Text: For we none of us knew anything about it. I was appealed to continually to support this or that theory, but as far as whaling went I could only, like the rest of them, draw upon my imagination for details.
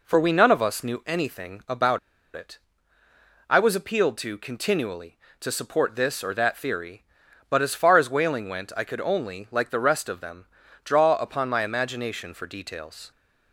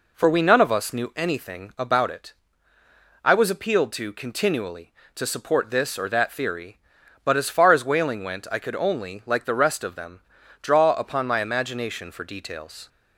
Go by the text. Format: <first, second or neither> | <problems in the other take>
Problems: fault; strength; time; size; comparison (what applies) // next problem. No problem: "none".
second | pauses between "about" and "it"; slight; at 1.9 s; 0.35 s long